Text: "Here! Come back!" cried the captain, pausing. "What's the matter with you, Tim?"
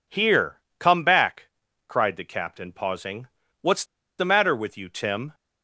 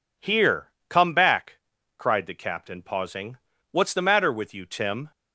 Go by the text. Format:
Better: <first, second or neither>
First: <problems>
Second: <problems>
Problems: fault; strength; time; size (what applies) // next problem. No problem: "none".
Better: second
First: pauses between "What's" and "the"; slight; at 3.8 s; 0.35 s long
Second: none